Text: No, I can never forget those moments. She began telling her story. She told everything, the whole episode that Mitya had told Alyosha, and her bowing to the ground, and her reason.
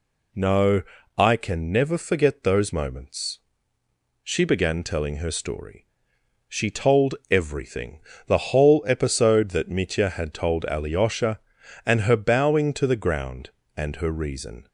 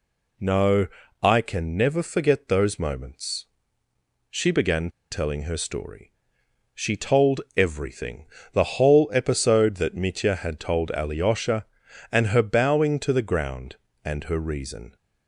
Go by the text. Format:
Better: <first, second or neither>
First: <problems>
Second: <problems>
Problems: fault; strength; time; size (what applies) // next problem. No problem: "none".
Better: first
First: none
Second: pauses between "began" and "telling"; slight; at 4.9 s; 0.20 s long